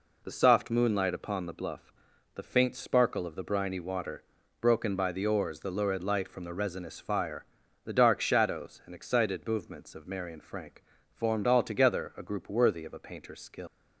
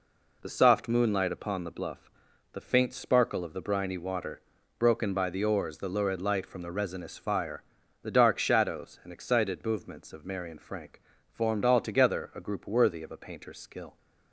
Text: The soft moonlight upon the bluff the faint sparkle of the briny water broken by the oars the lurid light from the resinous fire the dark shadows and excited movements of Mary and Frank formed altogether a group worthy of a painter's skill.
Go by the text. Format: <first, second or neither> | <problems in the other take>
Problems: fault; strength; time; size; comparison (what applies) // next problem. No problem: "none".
second | pauses between "bluff" and "the"; at 1.9 s; 0.44 s long; also in the second // pauses between "water" and "broken"; at 4.2 s; 0.40 s long; also in the second // pauses between "fire" and "the"; at 7.4 s; 0.42 s long; also in the second // pauses between "Frank" and "formed"; slight; at 10.8 s; 0.28 s long; slight in the second // leaves "skill" unfinished; at 13.6 s; 120 ms